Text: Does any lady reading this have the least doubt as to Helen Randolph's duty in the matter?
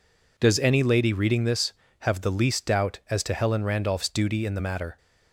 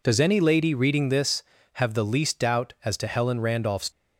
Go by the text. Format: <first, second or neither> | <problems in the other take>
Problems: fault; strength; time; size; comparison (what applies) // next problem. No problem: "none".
first | stops before "duty in the matter"; at 3.9 s